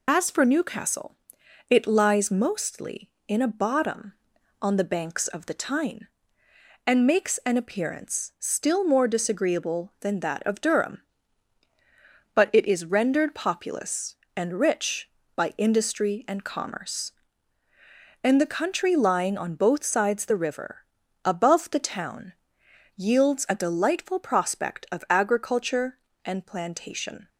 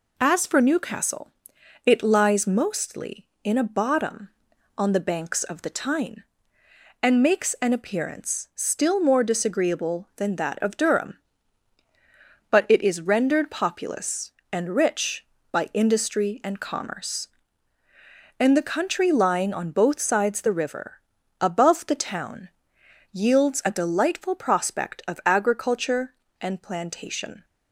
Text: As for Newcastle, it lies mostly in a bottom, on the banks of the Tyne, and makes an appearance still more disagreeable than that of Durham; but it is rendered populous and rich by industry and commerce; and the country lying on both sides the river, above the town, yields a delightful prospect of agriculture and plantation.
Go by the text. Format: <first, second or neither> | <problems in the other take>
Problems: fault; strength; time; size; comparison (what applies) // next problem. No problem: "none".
second | loses the start of "As"; at 0.0 s; 55 ms